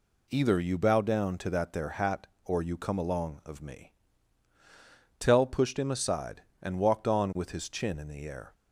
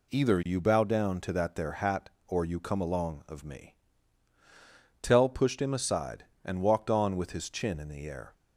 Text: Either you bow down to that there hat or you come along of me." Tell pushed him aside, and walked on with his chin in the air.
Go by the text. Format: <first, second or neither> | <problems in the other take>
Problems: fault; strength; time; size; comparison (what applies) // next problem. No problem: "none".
neither | none